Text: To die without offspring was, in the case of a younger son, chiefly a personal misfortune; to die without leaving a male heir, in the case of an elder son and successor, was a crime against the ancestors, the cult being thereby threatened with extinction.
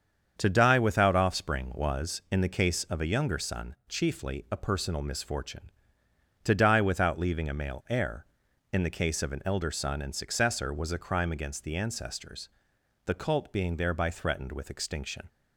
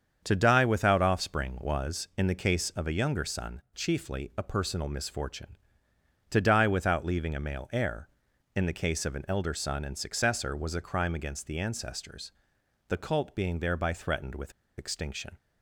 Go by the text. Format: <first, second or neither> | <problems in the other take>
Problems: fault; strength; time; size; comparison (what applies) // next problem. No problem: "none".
first | starts louder than the rest; strong; until 1.2 s; 7 dB; strong in the first // pauses between "with" and "extinction"; slight; at 14.5 s; 0.25 s long